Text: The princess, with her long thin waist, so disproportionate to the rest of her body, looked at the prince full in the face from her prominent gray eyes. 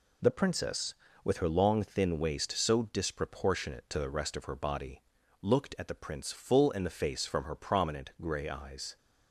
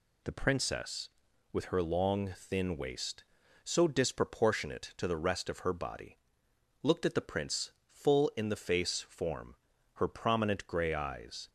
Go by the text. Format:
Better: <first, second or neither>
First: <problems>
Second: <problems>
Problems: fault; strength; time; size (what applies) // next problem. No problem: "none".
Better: first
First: none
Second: pauses between "prince" and "full"; slight; at 7.7 s; 0.20 s long // says "form" for "from"; at 9.0 s